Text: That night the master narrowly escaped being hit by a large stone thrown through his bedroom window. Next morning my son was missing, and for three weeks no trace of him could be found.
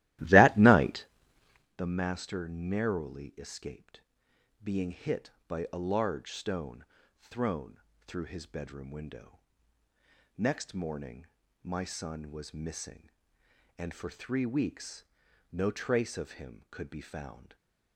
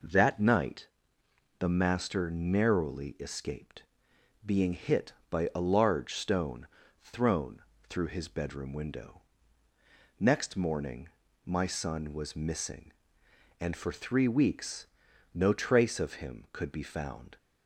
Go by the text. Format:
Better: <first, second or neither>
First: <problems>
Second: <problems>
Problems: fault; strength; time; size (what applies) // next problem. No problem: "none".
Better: second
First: starts louder than the rest; strong; until 1.7 s; 15.5 dB // pauses between "night" and "the"; noticeable; at 1.0 s; 0.72 s long // pauses between "escaped" and "being"; noticeable; at 4.0 s; 0.60 s long // pauses between "stone" and "thrown"; at 6.8 s; 0.38 s long // pauses between "thrown" and "through"; slight; at 7.7 s; 0.26 s long // pauses between "morning" and "my"; at 11.2 s; 0.38 s long // pauses between "weeks" and "no"; noticeable; at 15.0 s; 0.46 s long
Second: pauses between "night" and "the"; noticeable; at 0.8 s; 0.72 s long // pauses between "escaped" and "being"; noticeable; at 3.8 s; 0.60 s long // pauses between "stone" and "thrown"; at 6.6 s; 0.38 s long // pauses between "thrown" and "through"; slight; at 7.6 s; 0.26 s long // pauses between "morning" and "my"; at 11.0 s; 0.38 s long // pauses between "weeks" and "no"; noticeable; at 14.8 s; 0.46 s long